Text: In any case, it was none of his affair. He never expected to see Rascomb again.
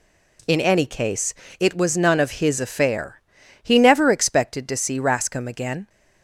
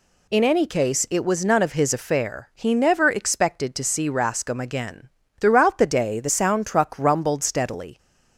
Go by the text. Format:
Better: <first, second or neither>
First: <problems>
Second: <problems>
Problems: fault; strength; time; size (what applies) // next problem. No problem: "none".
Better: first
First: none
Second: goes on to say "Throughout the day the sound truck rumbled steadily"; strong; from 5.3 s on; 2.5 s long